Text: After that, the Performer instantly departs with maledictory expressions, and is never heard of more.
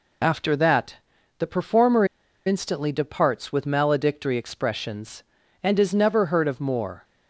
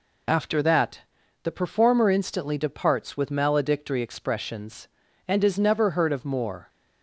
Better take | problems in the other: second | pauses between "Performer" and "instantly"; at 2.0 s; 0.41 s long

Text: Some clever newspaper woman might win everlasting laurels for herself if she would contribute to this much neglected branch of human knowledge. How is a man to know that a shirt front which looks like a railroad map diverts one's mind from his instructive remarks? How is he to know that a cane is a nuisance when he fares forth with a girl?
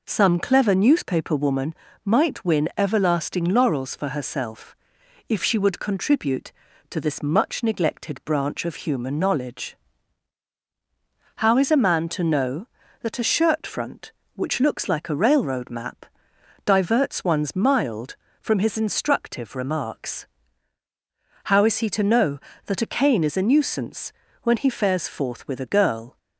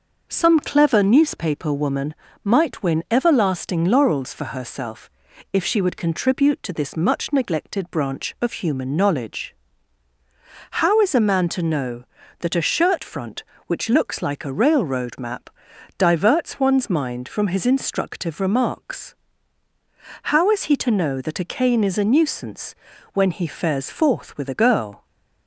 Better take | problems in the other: second | pauses between "woman" and "might"; slight; at 1.7 s; 0.30 s long; slight in the second // pauses between "herself" and "if"; noticeable; at 4.7 s; 0.54 s long; also in the second // pauses between "map" and "diverts"; noticeable; at 16.0 s; 0.60 s long; noticeable in the second // says "mild" for "mind"; at 17.5 s // pauses between "nuisance" and "when"; slight; at 24.1 s; 0.30 s long; also in the second

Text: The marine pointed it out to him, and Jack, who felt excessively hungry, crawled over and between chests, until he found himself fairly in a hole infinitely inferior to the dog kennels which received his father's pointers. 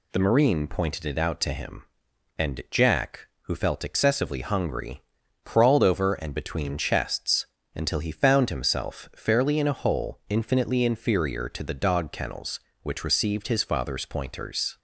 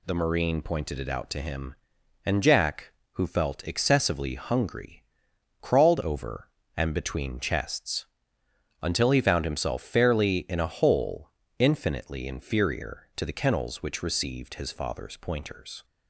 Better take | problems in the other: first | pauses between "hole" and "infinitely"; slight; at 11.2 s; 0.30 s long // skips "dog"; at 13.3 s

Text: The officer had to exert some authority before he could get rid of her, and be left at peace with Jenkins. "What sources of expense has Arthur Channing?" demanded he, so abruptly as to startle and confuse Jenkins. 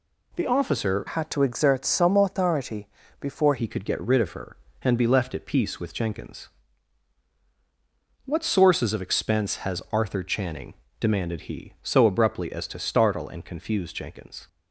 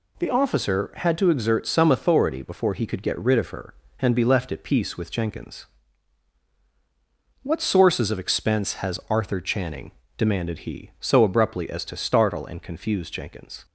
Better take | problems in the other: second | changes voice from "had" to "before"; from 1.0 to 3.5 s; 2.5 s long // pauses between "authority" and "before"; slight; at 2.8 s; 0.34 s long

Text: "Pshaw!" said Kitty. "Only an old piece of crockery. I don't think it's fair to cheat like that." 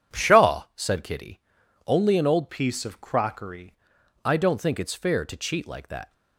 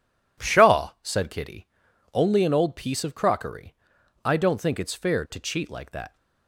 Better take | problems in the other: second | changes voice from "piece" to "crockery"; from 2.4 to 3.7 s; 1.3 s long

